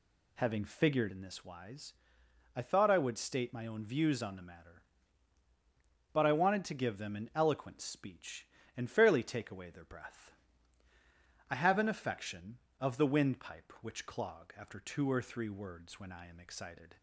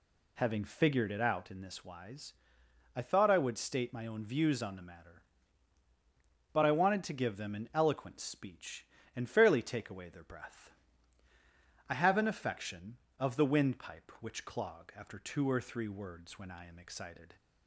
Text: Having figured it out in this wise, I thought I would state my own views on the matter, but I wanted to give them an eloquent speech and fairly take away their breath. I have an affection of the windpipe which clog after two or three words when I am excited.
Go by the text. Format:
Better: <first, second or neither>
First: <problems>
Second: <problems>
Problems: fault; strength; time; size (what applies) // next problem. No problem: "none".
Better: second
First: skips "it out"; at 1.0 s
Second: none